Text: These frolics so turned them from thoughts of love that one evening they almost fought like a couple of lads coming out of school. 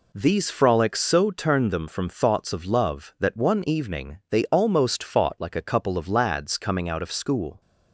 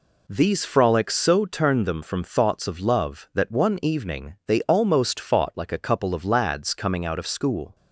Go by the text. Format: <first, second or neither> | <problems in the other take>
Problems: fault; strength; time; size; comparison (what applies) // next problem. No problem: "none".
neither | none